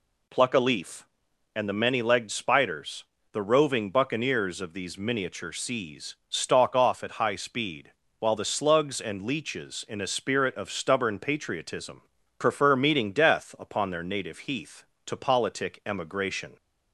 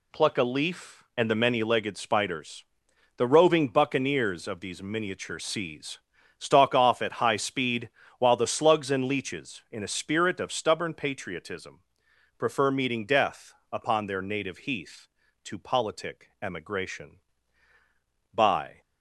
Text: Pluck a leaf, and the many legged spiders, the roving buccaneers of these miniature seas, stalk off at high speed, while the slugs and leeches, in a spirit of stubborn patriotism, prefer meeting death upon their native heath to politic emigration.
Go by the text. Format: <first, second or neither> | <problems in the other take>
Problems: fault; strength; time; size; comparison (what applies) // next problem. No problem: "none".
first | pauses between "death" and "upon"; slight; at 13.5 s; 0.18 s long // goes on to say "By"; slight; from 18.3 s on; 0.46 s long